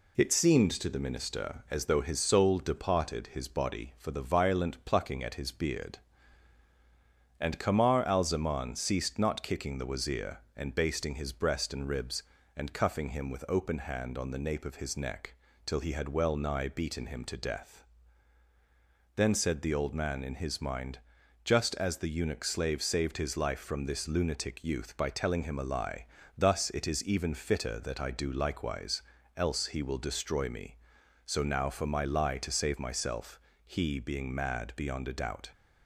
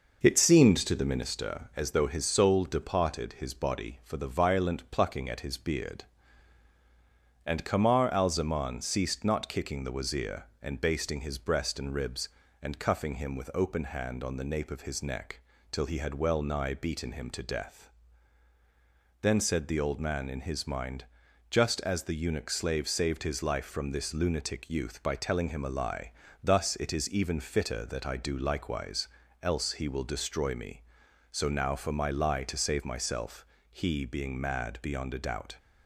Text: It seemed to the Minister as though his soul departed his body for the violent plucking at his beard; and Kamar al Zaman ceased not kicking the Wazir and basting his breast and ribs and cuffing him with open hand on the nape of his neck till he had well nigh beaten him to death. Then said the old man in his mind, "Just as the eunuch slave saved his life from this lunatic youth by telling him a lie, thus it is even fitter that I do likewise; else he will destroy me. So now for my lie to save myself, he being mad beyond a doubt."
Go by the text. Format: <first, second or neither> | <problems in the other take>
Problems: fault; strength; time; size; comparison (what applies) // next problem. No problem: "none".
first | starts louder than the rest; noticeable; until 1.4 s; 5.5 dB // pauses between "neck" and "till"; slight; at 15.3 s; 0.32 s long; slight in the first